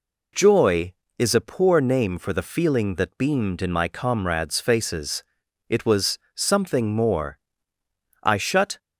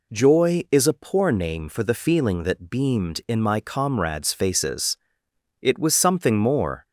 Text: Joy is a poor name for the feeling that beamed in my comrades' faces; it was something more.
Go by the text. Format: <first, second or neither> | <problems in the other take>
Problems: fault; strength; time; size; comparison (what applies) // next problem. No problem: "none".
second | pauses between "was" and "something"; slight; at 6.1 s; 0.16 s long // goes on to say "I shut"; from 8.2 s on; 0.56 s long